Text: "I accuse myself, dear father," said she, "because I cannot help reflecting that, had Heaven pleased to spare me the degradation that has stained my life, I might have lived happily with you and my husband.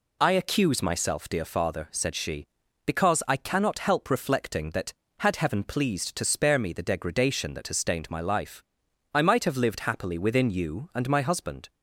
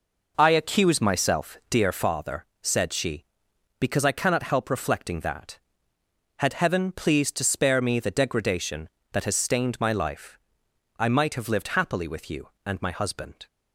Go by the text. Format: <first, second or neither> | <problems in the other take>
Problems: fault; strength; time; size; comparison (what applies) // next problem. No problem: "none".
second | says "within" for "with"; at 10.1 s